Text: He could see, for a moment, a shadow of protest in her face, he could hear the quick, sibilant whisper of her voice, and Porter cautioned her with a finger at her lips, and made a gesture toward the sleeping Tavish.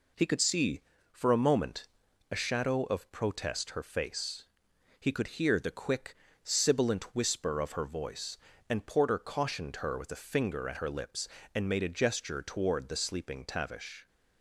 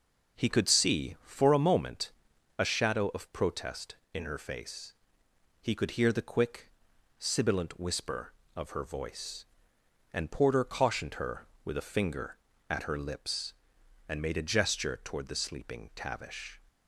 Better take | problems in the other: second | skips "in"; at 3.7 s

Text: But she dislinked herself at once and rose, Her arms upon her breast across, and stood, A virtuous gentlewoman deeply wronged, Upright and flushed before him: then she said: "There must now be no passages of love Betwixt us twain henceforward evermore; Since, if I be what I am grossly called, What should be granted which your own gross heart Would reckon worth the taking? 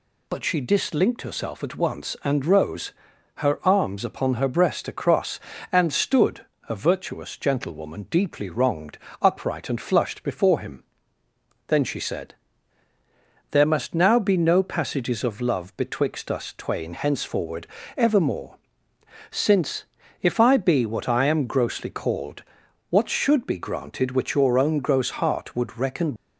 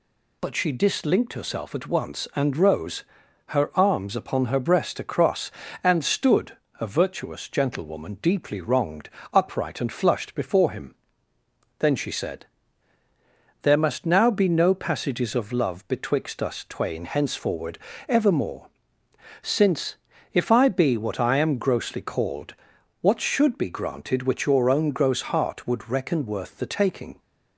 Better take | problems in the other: second | pauses between "henceforward" and "evermore"; slight; at 17.6 s; 0.28 s long; slight in the second // stops before "worth the taking"; at 26.1 s

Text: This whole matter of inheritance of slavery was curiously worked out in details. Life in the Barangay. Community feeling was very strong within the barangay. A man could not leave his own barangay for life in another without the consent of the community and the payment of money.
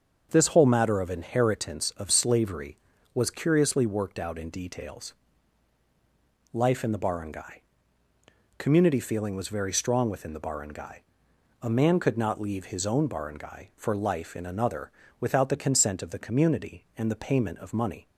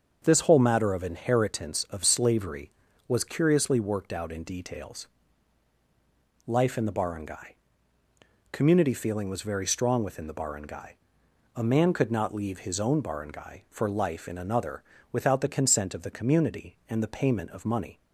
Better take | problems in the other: neither | starts louder than the rest; the same in both // pauses between "another" and "without"; slight; the same in both

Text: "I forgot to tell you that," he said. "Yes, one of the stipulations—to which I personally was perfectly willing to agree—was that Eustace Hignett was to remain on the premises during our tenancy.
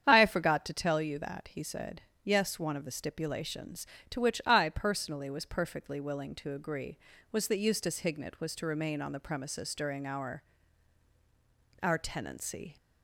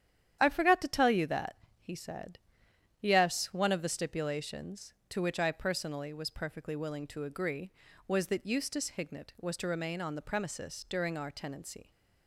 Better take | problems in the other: second | starts louder than the rest; strong; until 1.0 s; 8.5 dB; strong in the second // says "our" twice; at 11.8 s

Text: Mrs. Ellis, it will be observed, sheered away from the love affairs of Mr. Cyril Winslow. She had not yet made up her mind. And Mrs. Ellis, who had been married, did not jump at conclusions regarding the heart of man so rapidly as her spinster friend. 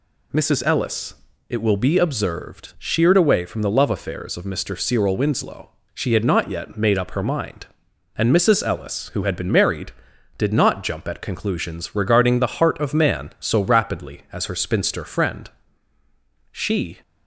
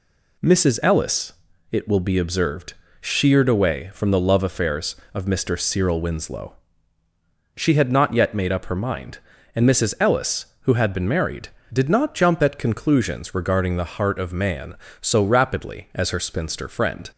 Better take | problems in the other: second | goes on to say "She"; slight; from 16.5 s on; 0.46 s long

